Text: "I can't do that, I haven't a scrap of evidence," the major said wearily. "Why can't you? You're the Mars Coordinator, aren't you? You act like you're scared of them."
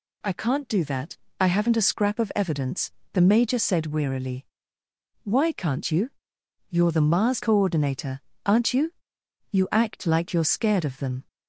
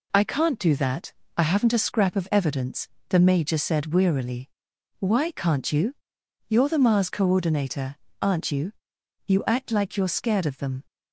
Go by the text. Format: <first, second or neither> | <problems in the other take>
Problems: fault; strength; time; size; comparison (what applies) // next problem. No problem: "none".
neither | none